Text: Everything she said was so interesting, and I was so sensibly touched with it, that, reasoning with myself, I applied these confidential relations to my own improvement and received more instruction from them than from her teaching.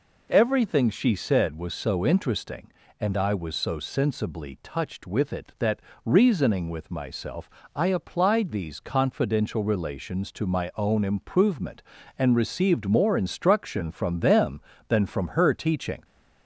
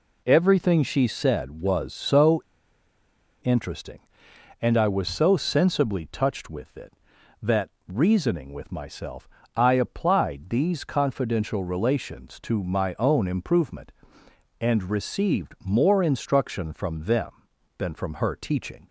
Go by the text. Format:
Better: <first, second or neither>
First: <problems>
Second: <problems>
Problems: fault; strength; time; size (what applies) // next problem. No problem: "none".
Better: first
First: none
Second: pauses between "so" and "interesting"; at 2.4 s; 1.0 s long